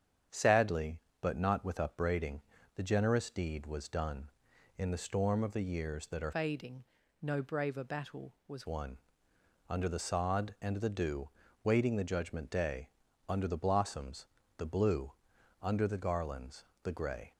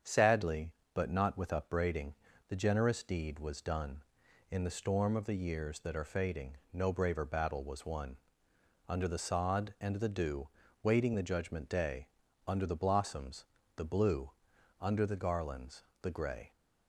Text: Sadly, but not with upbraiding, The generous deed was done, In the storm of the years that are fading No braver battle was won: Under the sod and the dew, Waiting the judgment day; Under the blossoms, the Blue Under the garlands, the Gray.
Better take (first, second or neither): second